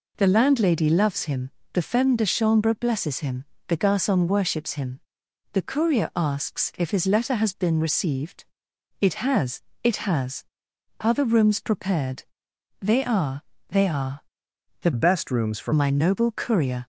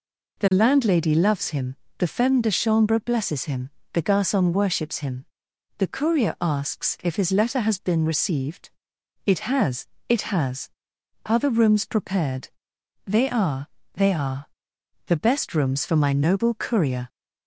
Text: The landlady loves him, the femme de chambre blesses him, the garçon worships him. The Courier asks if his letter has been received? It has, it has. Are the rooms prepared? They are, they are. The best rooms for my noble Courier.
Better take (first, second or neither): second